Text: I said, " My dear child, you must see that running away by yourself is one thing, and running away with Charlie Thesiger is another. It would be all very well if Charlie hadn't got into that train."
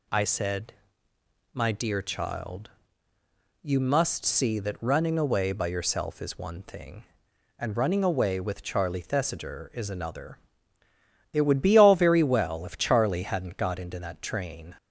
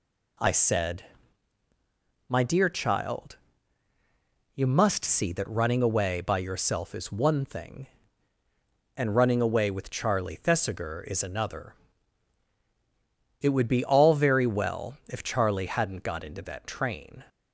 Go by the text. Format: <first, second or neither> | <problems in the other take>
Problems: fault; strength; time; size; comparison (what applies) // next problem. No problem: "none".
neither | none